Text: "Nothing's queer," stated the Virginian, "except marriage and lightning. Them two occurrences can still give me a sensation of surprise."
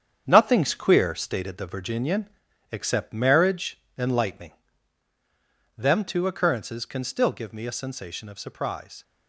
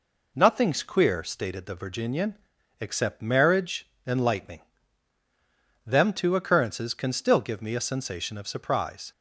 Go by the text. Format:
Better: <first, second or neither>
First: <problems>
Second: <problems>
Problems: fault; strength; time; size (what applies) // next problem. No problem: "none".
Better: second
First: gets quieter; strong; throughout; 7.5 dB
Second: none